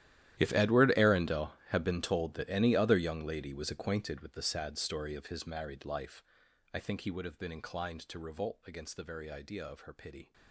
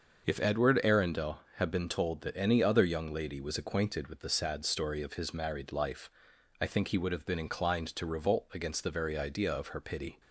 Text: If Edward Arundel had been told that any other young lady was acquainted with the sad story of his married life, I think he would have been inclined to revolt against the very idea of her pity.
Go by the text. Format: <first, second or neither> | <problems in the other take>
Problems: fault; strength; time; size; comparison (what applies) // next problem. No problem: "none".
second | gets quieter; strong; throughout; 19 dB // starts louder than the rest; strong; until 1.4 s; 12.5 dB; also in the second